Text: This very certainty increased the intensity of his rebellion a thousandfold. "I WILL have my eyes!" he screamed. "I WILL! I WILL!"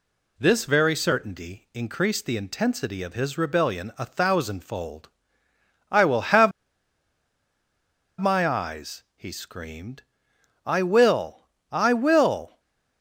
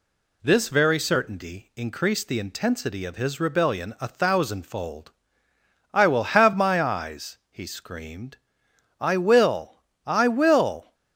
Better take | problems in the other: second | pauses between "have" and "my"; strong; at 6.5 s; 1.6 s long // stays silent after the last word; slight; from 12.4 s on; 0.6 s long

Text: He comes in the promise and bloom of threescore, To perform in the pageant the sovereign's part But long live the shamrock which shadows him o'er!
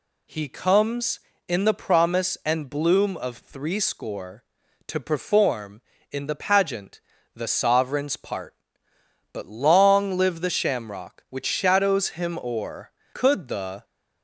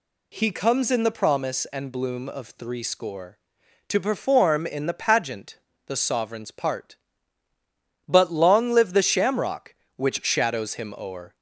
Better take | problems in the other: second | pauses between "pageant" and "the"; slight; at 6.9 s; 0.34 s long; slight in the second // goes on to say "Could the"; noticeable; from 13.1 s on; 0.70 s long

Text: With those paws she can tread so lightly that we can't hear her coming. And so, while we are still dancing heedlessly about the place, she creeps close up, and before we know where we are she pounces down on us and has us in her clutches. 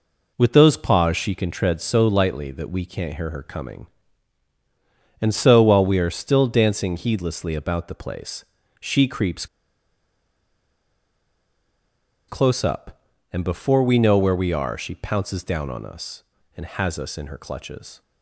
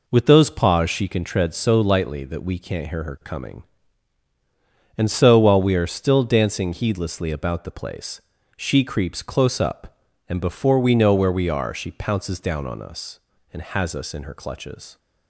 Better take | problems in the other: second | pauses between "creeps" and "close"; strong; at 9.4 s; 2.8 s long

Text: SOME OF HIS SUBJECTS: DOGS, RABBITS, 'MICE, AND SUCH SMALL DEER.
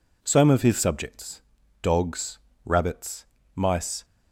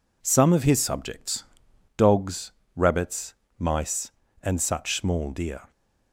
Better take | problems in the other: second | stops before "AND SUCH SMALL DEER"; at 4.0 s

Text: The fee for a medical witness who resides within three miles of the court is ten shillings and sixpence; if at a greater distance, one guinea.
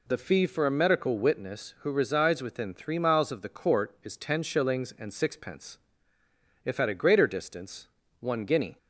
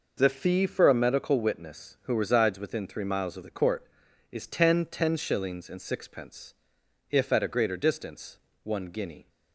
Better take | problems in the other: first | says "ten" twice; at 4.8 s

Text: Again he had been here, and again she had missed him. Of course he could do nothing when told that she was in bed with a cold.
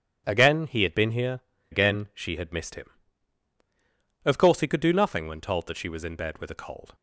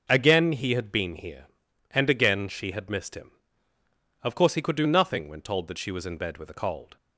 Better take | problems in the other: second | skips "and"; at 1.5 s

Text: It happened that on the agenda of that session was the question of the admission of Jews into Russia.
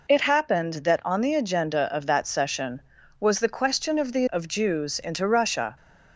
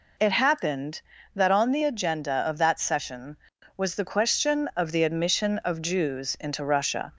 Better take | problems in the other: second | skips "admission"; at 4.2 s

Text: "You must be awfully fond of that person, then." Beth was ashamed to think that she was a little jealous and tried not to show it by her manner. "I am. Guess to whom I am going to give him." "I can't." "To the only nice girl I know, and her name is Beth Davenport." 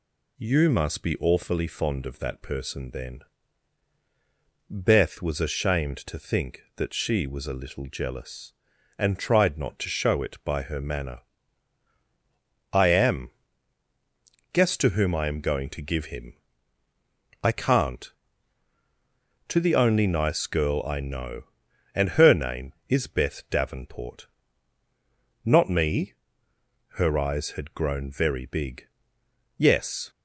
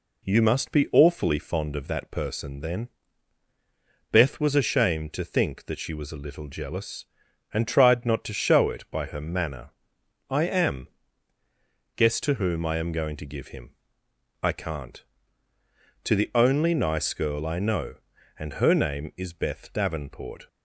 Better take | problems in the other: second | goes on to say "Not me Her eyes had grown very big Yes"; strong; from 25.4 s on; 4.6 s long

